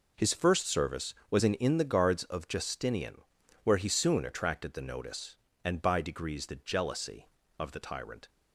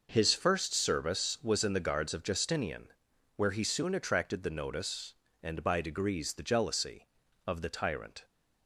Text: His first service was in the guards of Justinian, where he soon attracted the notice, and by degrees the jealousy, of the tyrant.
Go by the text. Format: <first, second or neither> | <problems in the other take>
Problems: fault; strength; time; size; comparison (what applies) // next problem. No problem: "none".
second | says "in" twice; at 1.5 s